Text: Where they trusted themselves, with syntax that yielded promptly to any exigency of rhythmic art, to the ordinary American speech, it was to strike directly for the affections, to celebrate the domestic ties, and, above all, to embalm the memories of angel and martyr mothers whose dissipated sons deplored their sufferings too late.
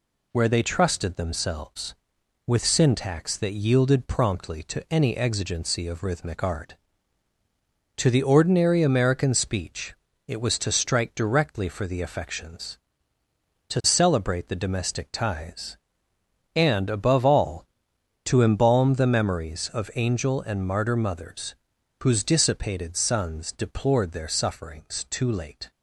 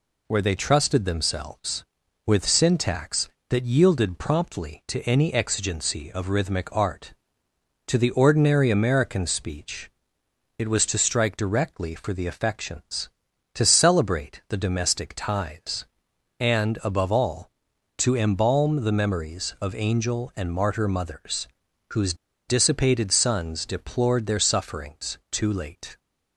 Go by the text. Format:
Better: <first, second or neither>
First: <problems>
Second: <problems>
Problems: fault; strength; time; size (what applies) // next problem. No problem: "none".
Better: first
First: pauses between "mothers" and "whose"; noticeable; at 21.5 s; 0.48 s long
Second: pauses between "mothers" and "whose"; noticeable; at 21.4 s; 0.46 s long // pauses between "whose" and "dissipated"; slight; at 22.1 s; 0.33 s long